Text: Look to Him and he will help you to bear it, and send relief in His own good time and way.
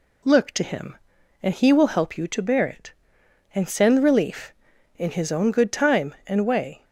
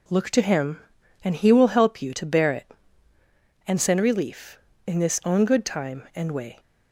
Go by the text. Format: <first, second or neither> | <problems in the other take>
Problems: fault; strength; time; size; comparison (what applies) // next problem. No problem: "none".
first | says "This" for "His"; at 4.9 s